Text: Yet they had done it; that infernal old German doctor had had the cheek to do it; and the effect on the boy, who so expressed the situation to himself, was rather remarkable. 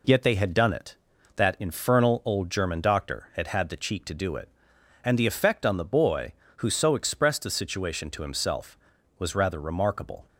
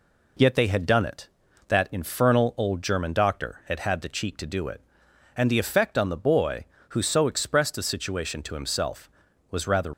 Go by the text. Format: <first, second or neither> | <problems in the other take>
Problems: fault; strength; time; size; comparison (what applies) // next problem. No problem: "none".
first | stops before "remarkable"; at 9.9 s